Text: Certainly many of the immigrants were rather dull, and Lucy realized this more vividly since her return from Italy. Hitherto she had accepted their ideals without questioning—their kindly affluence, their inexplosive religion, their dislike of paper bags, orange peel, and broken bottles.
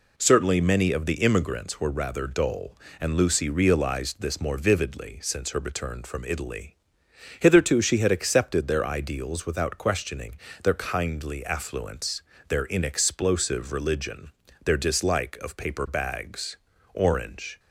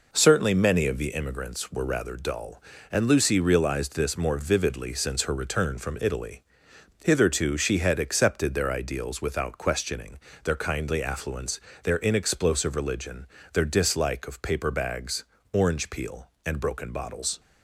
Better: second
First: stops before "peel and broken bottles"; at 17.5 s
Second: none

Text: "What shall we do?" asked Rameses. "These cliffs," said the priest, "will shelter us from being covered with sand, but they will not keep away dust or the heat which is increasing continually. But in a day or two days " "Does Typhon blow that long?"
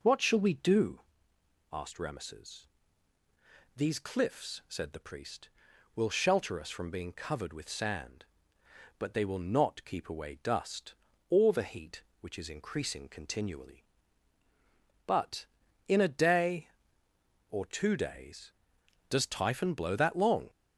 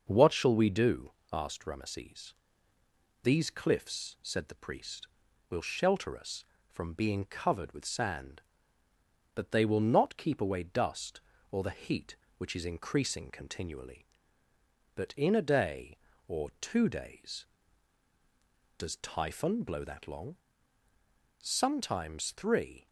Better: first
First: none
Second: goes on to say "Sometimes three"; from 21.4 s on; 1.4 s long

